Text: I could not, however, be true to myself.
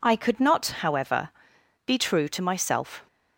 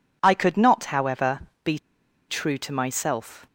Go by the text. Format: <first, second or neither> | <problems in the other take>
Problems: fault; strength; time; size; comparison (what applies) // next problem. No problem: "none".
first | pauses between "be" and "true"; noticeable; at 1.7 s; 0.51 s long